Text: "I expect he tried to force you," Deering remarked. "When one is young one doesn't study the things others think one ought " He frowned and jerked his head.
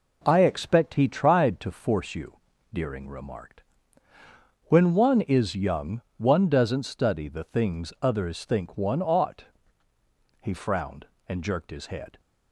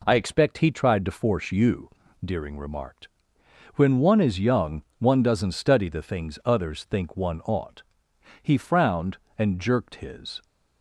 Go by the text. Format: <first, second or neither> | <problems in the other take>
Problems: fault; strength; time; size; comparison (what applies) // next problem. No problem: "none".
first | pauses between "young" and "one"; slight; at 4.8 s; 0.16 s long; slight in the first // stops before "head"; at 10.4 s